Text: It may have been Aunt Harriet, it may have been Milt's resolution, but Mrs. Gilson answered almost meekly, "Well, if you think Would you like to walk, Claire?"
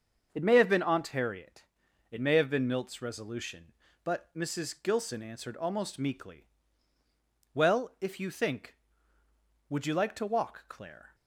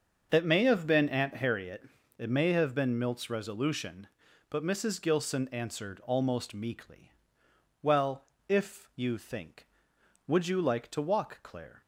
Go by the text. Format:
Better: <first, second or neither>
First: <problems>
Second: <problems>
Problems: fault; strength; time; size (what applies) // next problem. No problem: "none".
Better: neither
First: starts louder than the rest; until 1.3 s; 7 dB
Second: starts louder than the rest; until 1.3 s; 6.5 dB